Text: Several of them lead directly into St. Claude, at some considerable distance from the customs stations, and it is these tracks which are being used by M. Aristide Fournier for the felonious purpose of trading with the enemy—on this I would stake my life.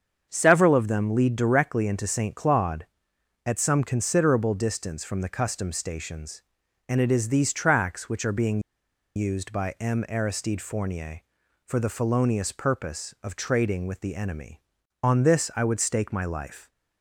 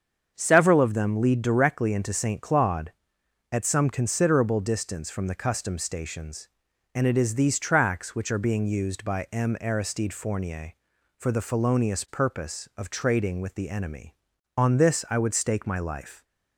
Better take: second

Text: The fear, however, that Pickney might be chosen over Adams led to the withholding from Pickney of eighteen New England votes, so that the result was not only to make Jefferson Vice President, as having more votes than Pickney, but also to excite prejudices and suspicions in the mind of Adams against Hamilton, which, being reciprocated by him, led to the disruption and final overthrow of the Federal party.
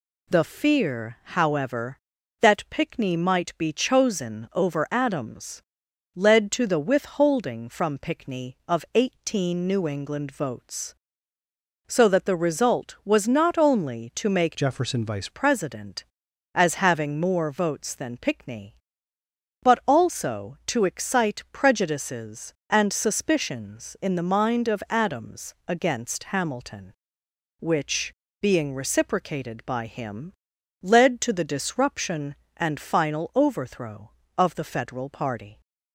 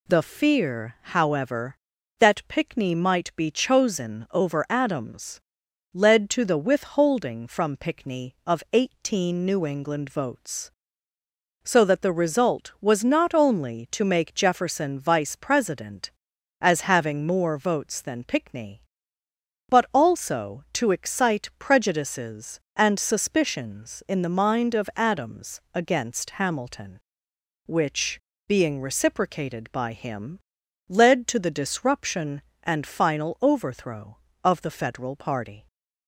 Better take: second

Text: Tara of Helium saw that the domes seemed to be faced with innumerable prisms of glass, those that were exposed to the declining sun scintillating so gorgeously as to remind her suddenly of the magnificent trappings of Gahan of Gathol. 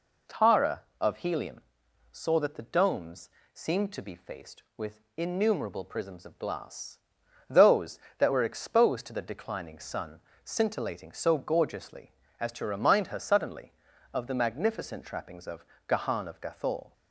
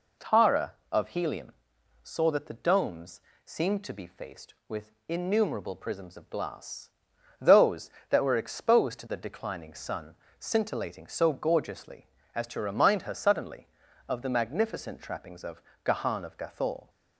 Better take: neither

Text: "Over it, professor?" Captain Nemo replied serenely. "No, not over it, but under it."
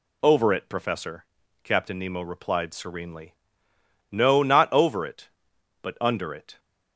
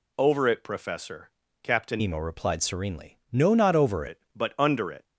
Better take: first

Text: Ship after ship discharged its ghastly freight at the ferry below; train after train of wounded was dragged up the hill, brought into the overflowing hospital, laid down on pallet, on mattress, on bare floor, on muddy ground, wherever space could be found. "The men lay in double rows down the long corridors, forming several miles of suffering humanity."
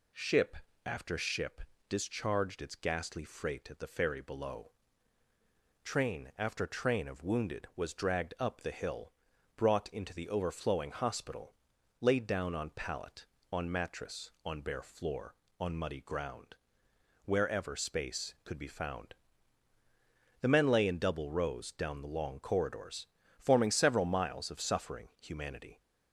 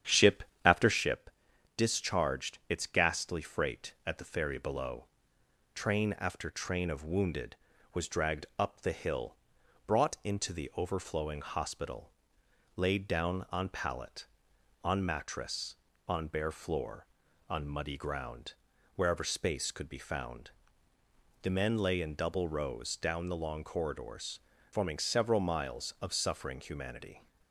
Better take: first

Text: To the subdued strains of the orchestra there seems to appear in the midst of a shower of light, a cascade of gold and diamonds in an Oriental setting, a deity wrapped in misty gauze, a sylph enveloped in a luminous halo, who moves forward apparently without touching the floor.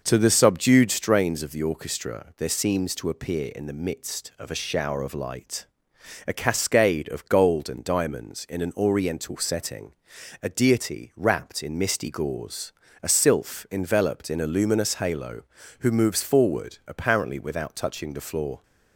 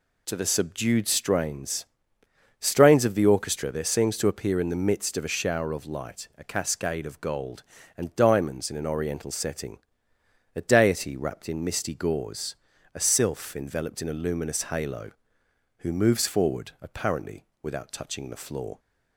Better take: first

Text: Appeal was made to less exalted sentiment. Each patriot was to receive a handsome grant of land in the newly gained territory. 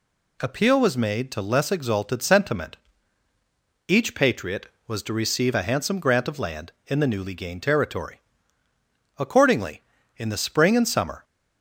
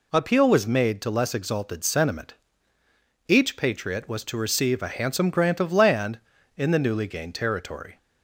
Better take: second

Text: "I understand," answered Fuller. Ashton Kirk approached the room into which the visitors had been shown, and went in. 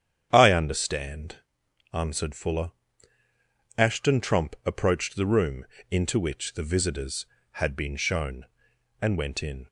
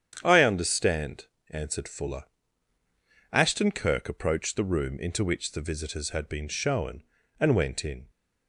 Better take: second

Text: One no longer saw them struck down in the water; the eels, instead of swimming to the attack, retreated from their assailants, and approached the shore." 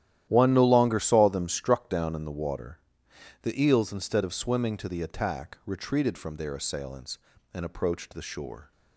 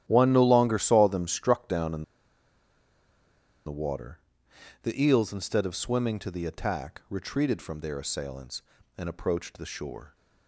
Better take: first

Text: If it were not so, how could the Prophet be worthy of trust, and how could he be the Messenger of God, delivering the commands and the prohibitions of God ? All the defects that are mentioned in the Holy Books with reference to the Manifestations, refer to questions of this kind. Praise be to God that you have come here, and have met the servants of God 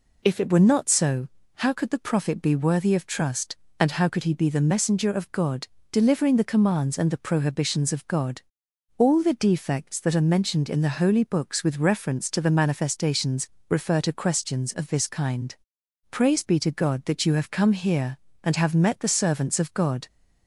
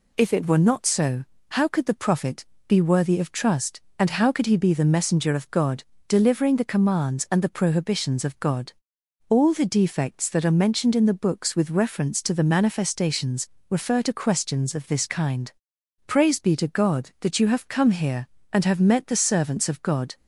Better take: first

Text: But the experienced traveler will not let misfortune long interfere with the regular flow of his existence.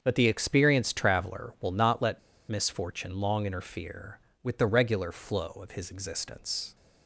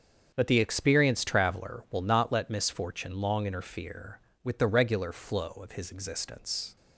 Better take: second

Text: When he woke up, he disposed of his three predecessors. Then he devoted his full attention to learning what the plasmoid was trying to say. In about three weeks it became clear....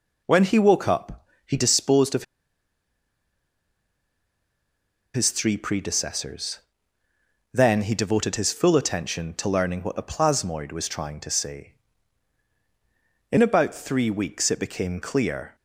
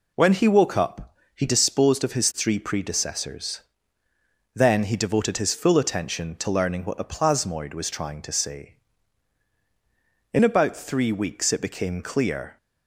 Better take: second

